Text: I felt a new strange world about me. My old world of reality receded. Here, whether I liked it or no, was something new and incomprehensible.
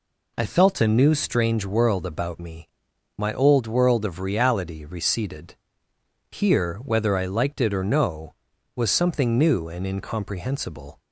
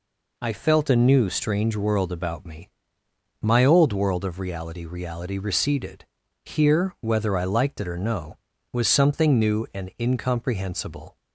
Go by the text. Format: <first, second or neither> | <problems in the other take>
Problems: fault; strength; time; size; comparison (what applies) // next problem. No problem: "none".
first | says "reality" twice; at 4.8 s